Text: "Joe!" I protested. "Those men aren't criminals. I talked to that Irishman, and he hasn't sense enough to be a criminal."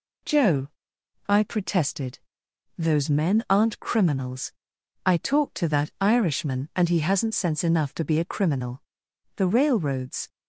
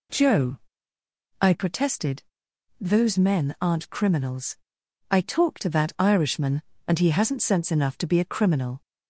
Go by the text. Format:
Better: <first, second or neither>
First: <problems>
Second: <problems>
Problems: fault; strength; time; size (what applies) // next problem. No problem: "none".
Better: second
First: goes on to say "The railroads"; noticeable; from 9.3 s on; 0.92 s long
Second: none